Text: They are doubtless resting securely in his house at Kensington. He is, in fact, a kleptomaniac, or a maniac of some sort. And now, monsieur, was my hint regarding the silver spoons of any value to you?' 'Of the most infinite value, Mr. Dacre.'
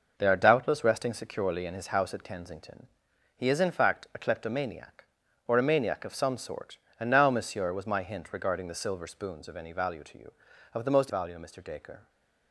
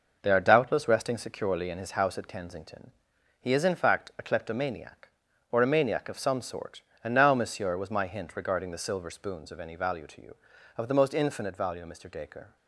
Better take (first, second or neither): second